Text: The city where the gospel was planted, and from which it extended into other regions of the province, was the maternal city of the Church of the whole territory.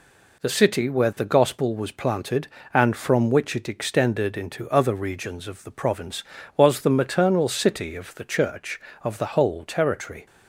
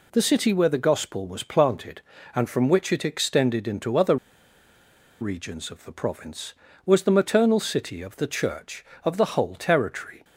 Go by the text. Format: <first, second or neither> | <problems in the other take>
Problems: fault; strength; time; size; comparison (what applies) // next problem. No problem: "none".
first | pauses between "other" and "regions"; at 4.1 s; 1.0 s long